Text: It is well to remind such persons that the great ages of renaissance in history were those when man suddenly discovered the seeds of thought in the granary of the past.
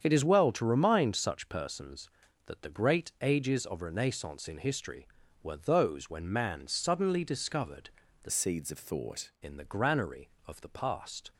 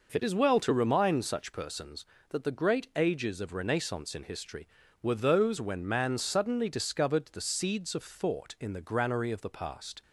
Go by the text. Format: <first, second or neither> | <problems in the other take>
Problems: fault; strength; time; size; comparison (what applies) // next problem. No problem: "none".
second | starts louder than the rest; strong; until 1.0 s; 8 dB // pauses between "discovered" and "the"; slight; at 7.8 s; 0.34 s long // changes voice from "seeds" to "thought"; from 8.3 to 9.3 s; 1.0 s long